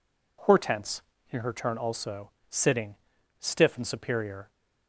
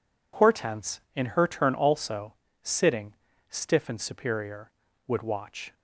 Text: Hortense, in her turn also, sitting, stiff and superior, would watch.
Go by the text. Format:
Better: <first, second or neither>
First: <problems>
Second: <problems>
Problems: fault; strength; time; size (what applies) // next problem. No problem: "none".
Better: second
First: stops before "would watch"; at 4.4 s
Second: none